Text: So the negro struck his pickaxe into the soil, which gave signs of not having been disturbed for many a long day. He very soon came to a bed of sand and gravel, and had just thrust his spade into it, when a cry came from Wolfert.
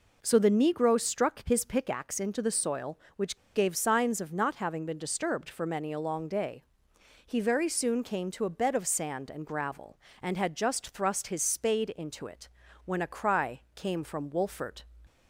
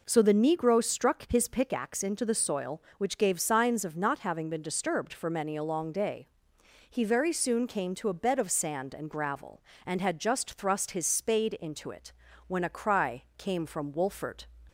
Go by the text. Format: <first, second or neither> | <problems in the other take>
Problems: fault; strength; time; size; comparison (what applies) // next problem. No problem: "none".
second | pauses between "which" and "gave"; slight; at 3.3 s; 0.18 s long